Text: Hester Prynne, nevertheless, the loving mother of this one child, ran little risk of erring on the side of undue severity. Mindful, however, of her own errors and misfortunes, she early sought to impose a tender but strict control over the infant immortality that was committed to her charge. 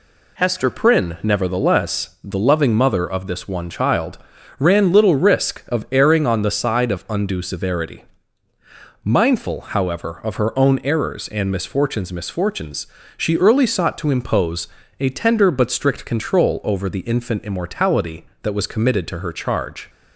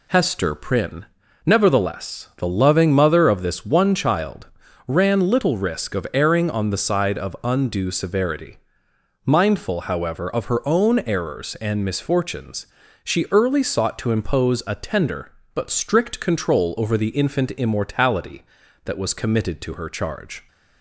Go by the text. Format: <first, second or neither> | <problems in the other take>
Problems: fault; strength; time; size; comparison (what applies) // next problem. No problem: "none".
second | says "misfortunes" twice; at 12.1 s // pauses between "impose" and "a"; slight; at 14.6 s; 0.32 s long